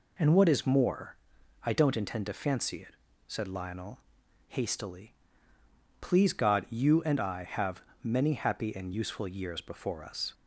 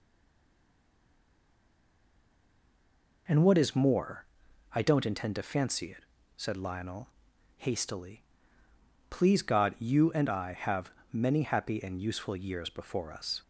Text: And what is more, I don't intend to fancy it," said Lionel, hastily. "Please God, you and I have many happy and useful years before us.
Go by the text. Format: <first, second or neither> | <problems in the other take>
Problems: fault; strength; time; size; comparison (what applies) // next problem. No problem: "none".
first | stays silent before the first word; strong; until 3.2 s; 3.2 s long // pauses between "have" and "many"; slight; at 10.9 s; 0.20 s long; slight in the first